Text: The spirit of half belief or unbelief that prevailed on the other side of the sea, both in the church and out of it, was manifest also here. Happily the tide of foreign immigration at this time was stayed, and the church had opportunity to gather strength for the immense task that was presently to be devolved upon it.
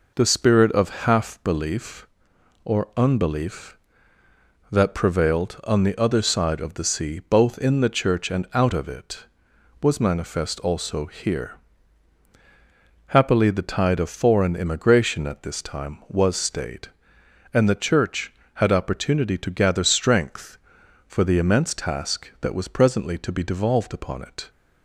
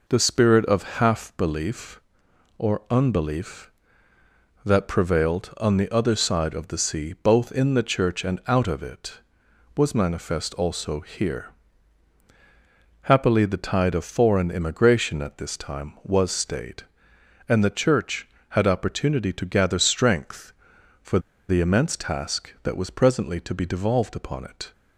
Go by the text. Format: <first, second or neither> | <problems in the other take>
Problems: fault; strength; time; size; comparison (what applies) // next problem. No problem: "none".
first | pauses between "for" and "the"; slight; at 21.1 s; 0.30 s long